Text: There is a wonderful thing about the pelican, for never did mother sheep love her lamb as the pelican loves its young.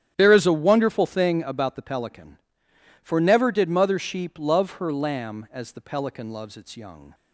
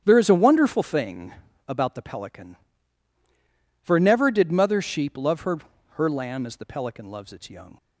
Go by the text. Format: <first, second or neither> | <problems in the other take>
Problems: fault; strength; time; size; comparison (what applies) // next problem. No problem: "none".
first | starts louder than the rest; strong; until 1.0 s; 10 dB; strong in the first // pauses between "thing" and "about"; at 1.3 s; 0.38 s long // says "her" twice; at 5.9 s